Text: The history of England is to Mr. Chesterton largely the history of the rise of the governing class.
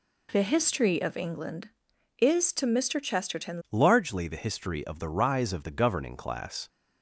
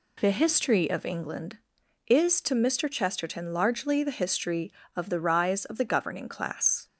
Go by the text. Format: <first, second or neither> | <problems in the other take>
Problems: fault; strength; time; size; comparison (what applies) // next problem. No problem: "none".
second | changes voice at "largely"; from 3.6 s on; 3.0 s long